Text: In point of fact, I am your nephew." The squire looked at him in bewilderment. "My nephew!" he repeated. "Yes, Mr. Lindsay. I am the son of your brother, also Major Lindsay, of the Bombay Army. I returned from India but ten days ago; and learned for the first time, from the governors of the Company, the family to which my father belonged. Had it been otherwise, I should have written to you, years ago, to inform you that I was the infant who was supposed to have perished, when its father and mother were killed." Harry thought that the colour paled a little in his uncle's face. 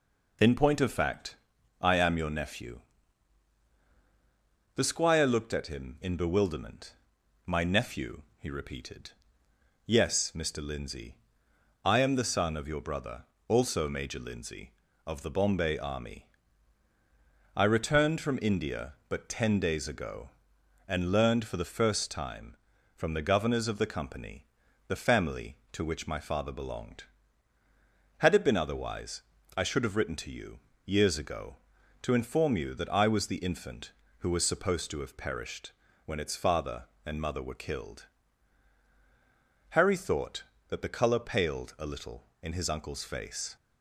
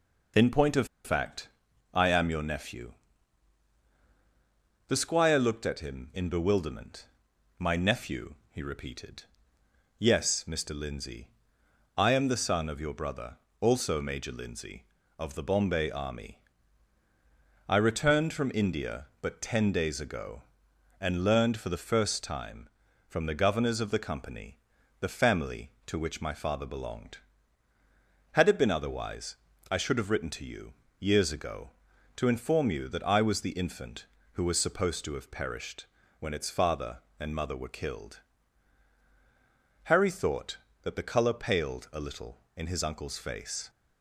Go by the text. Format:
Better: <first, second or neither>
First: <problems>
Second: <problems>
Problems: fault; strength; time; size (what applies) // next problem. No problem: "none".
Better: first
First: none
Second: pauses between "of" and "fact"; slight; at 0.8 s; 0.19 s long